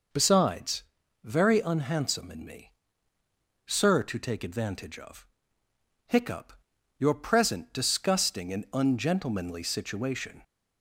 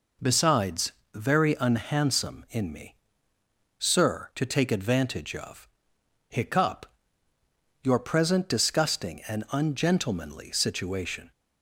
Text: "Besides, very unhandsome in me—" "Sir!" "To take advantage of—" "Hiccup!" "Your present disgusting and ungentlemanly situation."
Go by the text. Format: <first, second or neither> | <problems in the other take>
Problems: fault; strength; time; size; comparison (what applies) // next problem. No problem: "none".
neither | none